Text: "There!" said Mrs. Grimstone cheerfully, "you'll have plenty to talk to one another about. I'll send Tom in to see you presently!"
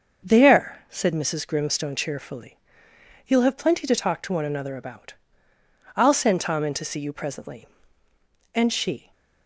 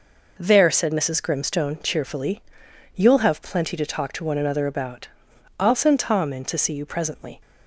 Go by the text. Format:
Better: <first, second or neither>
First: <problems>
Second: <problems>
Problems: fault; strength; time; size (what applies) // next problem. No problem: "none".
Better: second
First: starts louder than the rest; until 1.3 s; 6.5 dB // goes on to say "And she"; from 8.5 s on; 0.58 s long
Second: none